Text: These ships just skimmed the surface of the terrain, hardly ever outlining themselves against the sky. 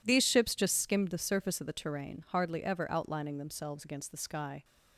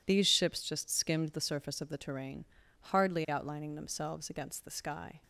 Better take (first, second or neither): first